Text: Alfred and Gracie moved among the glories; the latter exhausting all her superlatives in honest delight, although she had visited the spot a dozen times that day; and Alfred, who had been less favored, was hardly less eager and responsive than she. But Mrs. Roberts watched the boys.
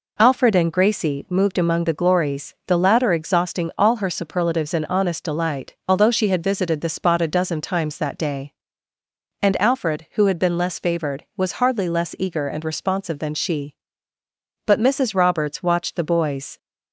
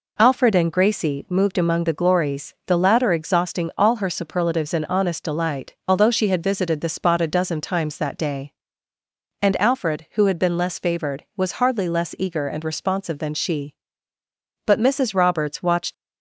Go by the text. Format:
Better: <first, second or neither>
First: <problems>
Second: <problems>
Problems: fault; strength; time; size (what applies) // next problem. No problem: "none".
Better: first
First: none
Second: stops before "the boys"; at 15.9 s